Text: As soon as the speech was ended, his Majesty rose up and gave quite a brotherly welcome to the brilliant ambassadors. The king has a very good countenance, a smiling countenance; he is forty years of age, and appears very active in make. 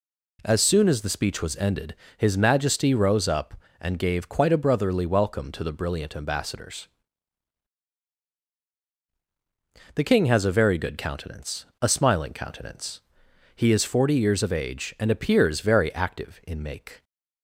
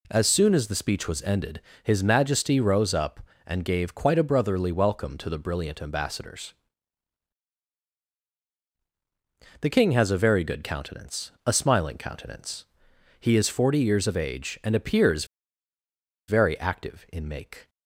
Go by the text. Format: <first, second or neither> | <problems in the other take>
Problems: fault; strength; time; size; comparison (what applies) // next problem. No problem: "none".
first | pauses between "appears" and "very"; at 15.2 s; 1.0 s long